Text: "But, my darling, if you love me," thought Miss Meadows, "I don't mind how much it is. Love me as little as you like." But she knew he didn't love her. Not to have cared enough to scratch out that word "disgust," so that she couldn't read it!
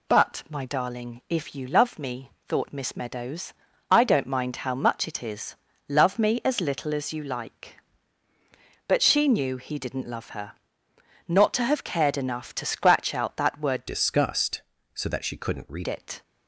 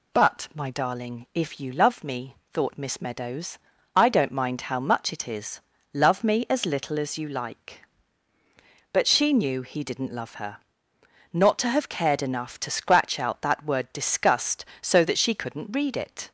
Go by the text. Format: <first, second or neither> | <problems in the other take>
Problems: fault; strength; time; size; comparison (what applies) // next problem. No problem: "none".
second | changes voice from "disgust" to "read"; from 13.8 to 15.8 s; 2.0 s long